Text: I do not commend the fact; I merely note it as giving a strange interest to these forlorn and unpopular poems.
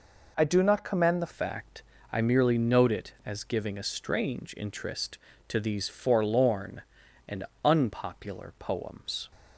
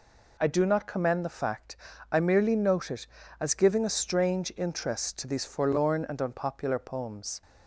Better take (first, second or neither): second